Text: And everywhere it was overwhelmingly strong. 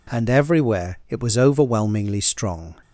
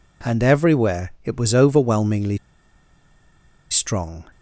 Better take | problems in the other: first | pauses between "overwhelmingly" and "strong"; strong; at 2.3 s; 1.3 s long

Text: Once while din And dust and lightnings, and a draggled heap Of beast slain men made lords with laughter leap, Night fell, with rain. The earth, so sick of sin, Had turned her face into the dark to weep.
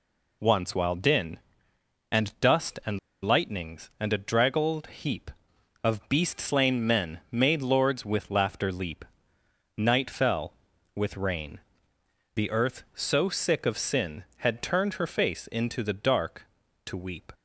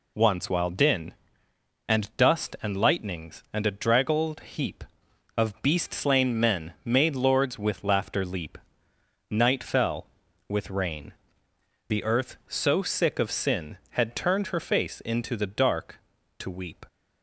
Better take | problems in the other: second | pauses between "and" and "lightnings"; slight; at 2.9 s; 0.23 s long

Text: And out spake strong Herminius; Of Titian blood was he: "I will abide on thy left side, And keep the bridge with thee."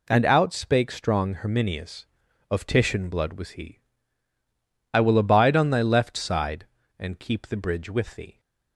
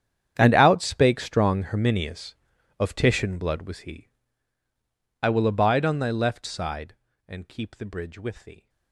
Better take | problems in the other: first | gets quieter; strong; throughout; 18.5 dB

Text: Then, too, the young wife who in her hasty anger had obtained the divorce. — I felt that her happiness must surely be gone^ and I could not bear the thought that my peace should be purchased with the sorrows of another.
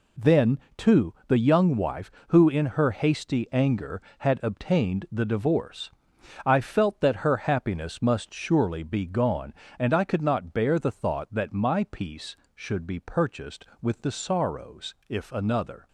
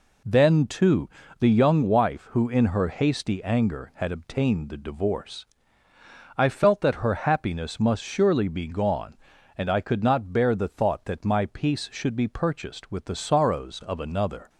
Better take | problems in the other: second | says "if" for "of"; at 15.0 s

